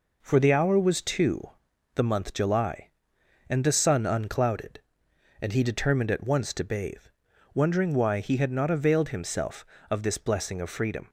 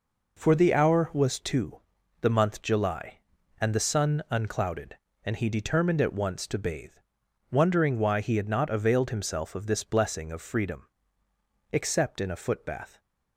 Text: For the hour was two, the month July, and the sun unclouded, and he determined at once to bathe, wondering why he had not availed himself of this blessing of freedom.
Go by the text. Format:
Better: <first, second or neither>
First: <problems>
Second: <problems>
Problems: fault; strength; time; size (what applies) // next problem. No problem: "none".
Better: first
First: none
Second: goes on to say "Except in a footbath"; noticeable; from 11.7 s on; 1.2 s long